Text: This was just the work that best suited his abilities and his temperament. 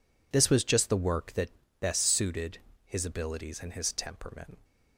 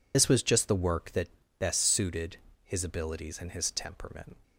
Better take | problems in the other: first | loses the start of "This"; at 0.1 s; 45 ms // pauses between "that" and "best"; slight; at 1.2 s; 0.30 s long; slight in the first // pauses between "suited" and "his"; slight; at 2.3 s; 0.28 s long; slight in the first

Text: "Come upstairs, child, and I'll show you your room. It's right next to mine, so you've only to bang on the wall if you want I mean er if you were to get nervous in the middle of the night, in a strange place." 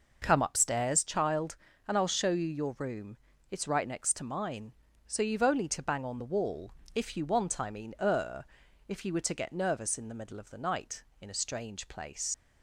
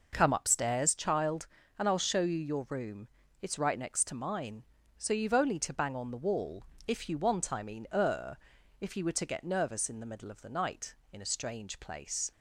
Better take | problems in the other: second | pauses between "wall" and "if"; slight; at 6.6 s; 0.24 s long; slight in the second // pauses between "er" and "if"; at 8.4 s; 0.42 s long; also in the second // leaves "place" unfinished; at 12.3 s; 50 ms

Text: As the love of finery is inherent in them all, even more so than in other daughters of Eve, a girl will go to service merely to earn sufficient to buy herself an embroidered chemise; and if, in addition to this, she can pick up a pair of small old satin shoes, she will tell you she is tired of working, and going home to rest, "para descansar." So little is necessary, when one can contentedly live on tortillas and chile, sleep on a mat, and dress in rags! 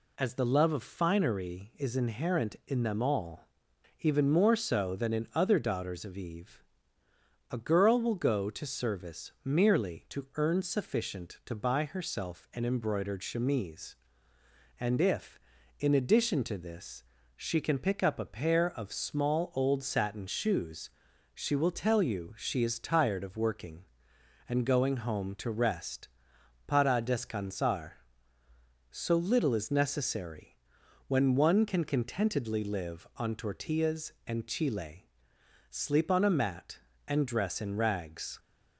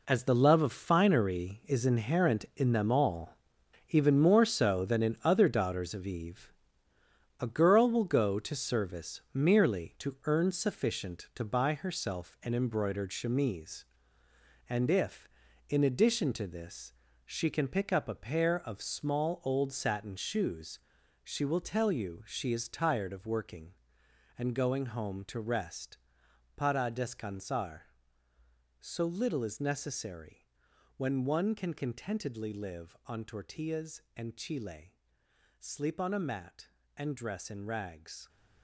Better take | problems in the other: first | gets quieter; strong; throughout; 11 dB

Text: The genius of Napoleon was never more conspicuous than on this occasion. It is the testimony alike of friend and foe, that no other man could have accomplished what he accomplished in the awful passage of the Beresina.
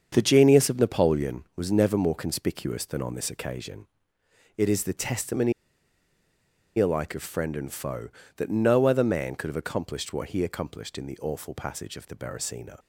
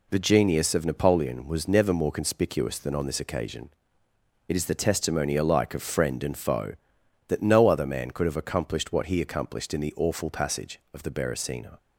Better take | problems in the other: second | starts louder than the rest; strong; until 1.1 s; 7 dB // pauses between "testimony" and "alike"; strong; at 5.5 s; 1.2 s long

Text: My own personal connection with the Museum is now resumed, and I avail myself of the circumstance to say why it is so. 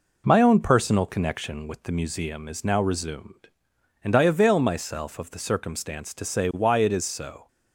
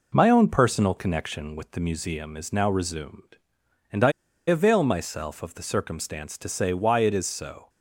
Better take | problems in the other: first | pauses between "I" and "avail"; slight; at 4.1 s; 0.36 s long

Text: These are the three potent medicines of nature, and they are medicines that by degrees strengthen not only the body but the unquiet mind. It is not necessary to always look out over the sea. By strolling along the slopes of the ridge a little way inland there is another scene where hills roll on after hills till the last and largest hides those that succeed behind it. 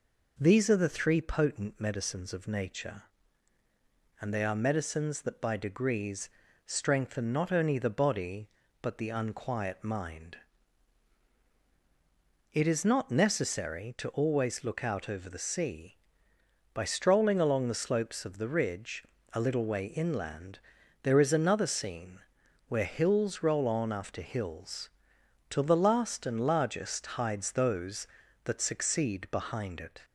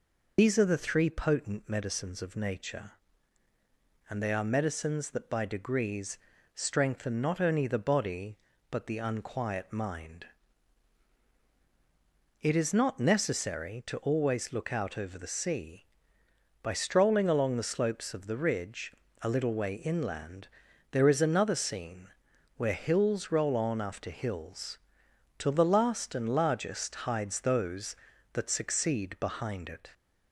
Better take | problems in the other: first | loses the start of "These"; at 0.3 s; 115 ms // pauses between "degrees" and "strengthen"; at 6.1 s; 0.38 s long; also in the first // pauses between "ridge" and "a"; slight; at 18.9 s; 0.28 s long; slight in the first // pauses between "inland" and "there"; at 20.4 s; 0.42 s long; also in the first // pauses between "scene" and "where"; noticeable; at 22.0 s; 0.50 s long; noticeable in the first // pauses between "hills" and "till"; noticeable; at 24.7 s; 0.58 s long; noticeable in the first

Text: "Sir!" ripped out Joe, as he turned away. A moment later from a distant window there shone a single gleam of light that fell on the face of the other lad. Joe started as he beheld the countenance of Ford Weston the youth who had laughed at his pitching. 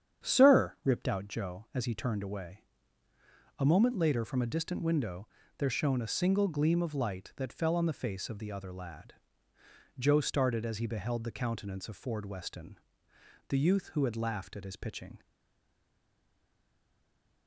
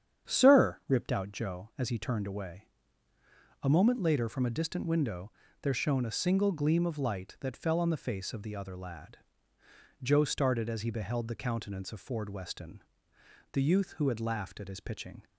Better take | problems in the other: second | starts louder than the rest; strong; until 1.3 s; 8.5 dB; strong in the second // pauses between "window" and "there"; slight; at 5.2 s; 0.32 s long; slight in the second // pauses between "Weston" and "the"; noticeable; at 12.7 s; 0.70 s long; noticeable in the second // stays silent after the last word; from 15.2 s on; 2.2 s long

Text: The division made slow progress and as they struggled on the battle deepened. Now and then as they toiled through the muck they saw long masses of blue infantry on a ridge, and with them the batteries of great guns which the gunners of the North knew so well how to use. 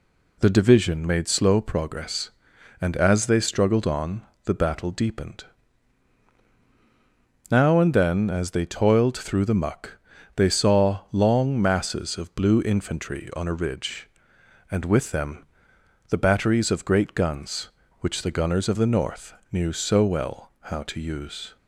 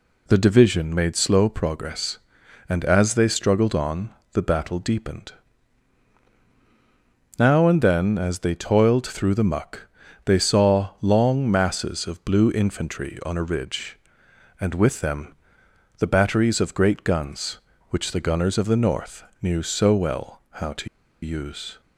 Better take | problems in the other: first | pauses between "on" and "the"; slight; at 4.0 s; 0.22 s long; slight in the first // pauses between "muck" and "they"; at 9.8 s; 0.38 s long; also in the first // pauses between "them" and "the"; noticeable; at 15.3 s; 0.62 s long; noticeable in the first // pauses between "North" and "knew"; slight; at 19.2 s; 0.20 s long; slight in the first // pauses between "to" and "use"; slight; at 20.8 s; 0.35 s long

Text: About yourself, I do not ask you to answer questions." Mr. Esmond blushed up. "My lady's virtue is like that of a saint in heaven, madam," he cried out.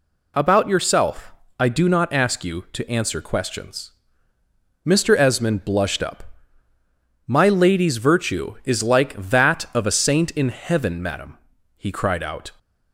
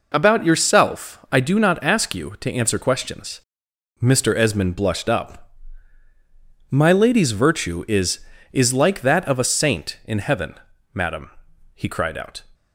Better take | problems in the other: first | says "is" twice; at 8.5 s

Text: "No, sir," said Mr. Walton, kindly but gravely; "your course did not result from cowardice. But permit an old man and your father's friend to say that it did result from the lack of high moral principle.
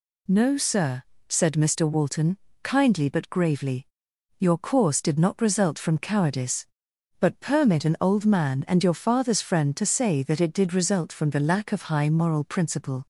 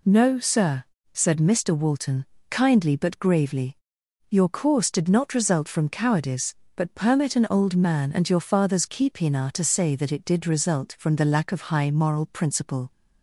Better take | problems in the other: first | says "keepina" for "friend"; at 8.8 s

